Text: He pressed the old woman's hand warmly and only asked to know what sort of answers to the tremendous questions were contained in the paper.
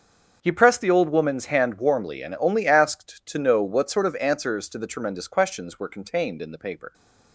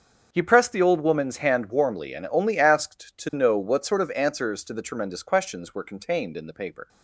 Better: neither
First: starts louder than the rest; until 1.4 s; 6.5 dB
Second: starts louder than the rest; until 1.3 s; 6.5 dB

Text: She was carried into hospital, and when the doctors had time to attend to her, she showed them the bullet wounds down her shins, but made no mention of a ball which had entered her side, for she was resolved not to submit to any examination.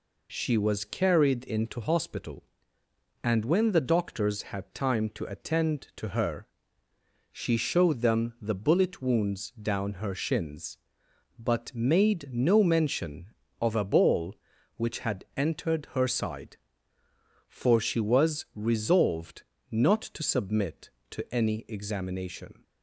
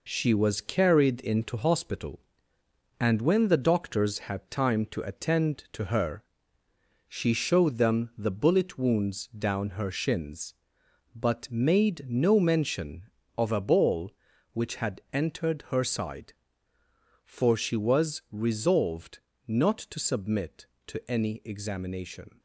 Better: first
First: pauses between "resolved" and "not"; slight; at 19.4 s; 0.26 s long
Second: gets quieter; noticeable; throughout; 6 dB // pauses between "resolved" and "not"; slight; at 19.1 s; 0.26 s long

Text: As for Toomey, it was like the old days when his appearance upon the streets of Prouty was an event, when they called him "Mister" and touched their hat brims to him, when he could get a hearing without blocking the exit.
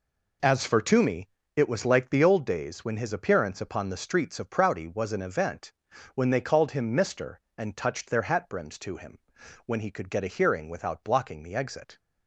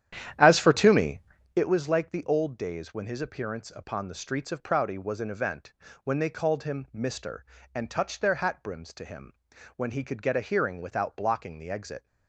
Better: first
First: none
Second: starts louder than the rest; strong; until 1.7 s; 10.5 dB

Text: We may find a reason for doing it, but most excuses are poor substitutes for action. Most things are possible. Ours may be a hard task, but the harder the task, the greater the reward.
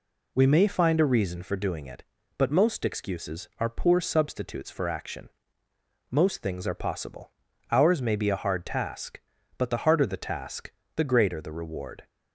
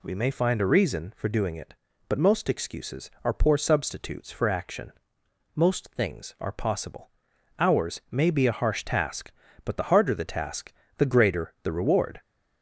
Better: first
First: none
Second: says "harsh" for "hard"; at 8.5 s

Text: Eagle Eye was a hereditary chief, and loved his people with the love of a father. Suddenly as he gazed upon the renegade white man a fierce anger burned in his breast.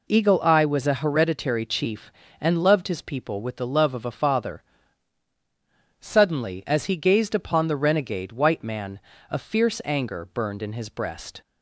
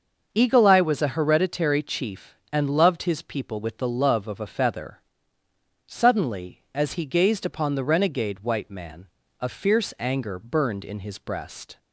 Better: first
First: pauses between "man" and "a"; slight; at 9.0 s; 0.28 s long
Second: starts louder than the rest; noticeable; until 1.3 s; 6 dB // says "feather" for "father"; at 4.4 s // pauses between "man" and "a"; slight; at 9.0 s; 0.32 s long

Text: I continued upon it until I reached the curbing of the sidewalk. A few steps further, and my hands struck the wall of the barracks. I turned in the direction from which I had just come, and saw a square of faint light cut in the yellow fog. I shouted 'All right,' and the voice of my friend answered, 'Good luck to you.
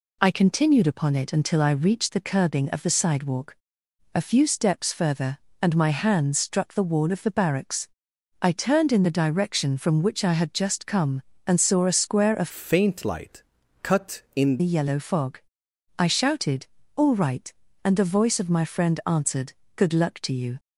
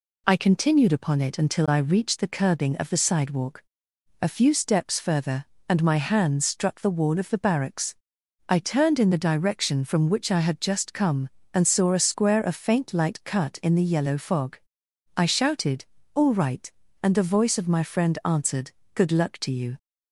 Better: second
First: changes voice from "faint" to "in"; from 12.5 to 14.5 s; 2.0 s long // pauses between "light" and "cut"; at 13.4 s; 0.40 s long // pauses between "shouted" and "All"; slight; at 16.6 s; 0.28 s long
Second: pauses between "shouted" and "All"; slight; at 15.8 s; 0.28 s long

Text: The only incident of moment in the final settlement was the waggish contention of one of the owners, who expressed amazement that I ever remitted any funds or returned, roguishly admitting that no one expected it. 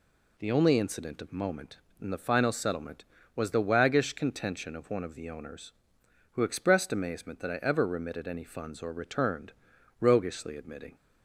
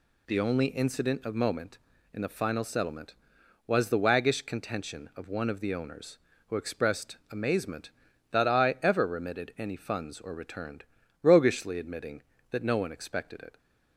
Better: second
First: stops before "that no one expected it"; at 10.9 s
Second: none

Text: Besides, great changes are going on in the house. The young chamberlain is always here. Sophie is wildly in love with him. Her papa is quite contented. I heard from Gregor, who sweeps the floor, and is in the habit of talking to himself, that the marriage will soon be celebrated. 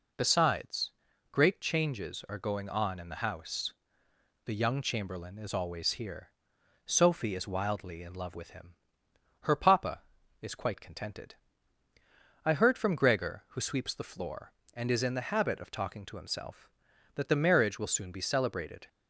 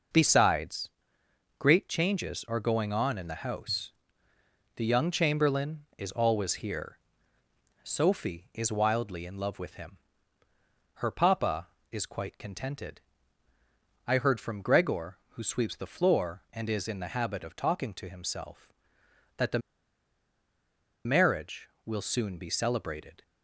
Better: first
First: none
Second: pauses between "the" and "marriage"; strong; at 19.5 s; 1.4 s long

